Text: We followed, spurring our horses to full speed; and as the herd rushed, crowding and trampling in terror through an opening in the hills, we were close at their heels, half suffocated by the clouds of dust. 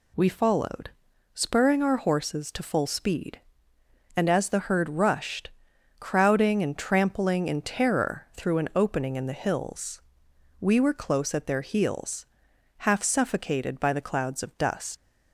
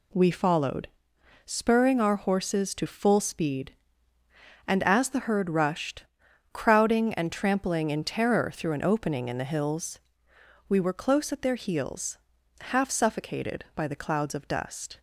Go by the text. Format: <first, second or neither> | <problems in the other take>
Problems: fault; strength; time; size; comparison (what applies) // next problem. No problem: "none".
second | leaves "dust" unfinished; at 14.9 s; 80 ms